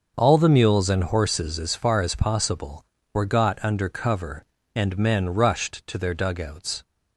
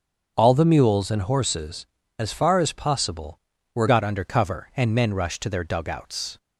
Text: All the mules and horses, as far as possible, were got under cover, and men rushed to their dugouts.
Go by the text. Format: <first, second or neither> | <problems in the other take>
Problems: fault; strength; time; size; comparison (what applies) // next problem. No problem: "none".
first | starts louder than the rest; until 1.3 s; 7 dB; noticeable in the first // changes voice at "got"; from 3.8 s on; 2.5 s long